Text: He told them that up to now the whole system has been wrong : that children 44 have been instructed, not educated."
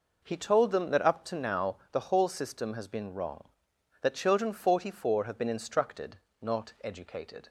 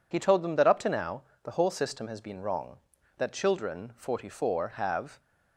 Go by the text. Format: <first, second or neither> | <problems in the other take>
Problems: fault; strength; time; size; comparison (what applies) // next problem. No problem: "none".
first | pauses between "now" and "the"; slight; at 1.2 s; 0.22 s long // stops before "been instructed not educated"; at 5.1 s